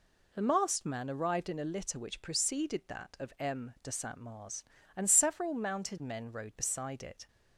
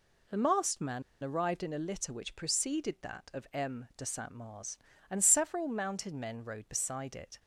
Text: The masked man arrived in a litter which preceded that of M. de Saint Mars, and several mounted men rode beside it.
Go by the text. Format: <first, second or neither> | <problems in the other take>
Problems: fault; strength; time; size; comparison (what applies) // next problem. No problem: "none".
first | pauses between "man" and "arrived"; slight; at 1.0 s; 0.21 s long